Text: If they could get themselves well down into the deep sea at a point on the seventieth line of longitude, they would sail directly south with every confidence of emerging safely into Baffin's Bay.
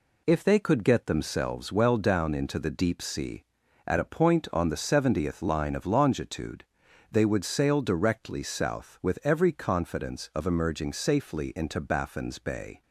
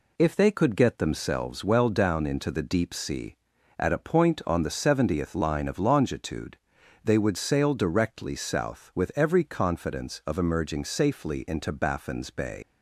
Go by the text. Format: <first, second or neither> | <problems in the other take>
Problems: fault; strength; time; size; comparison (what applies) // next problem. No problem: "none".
first | leaves "Bay" unfinished; at 12.6 s; 110 ms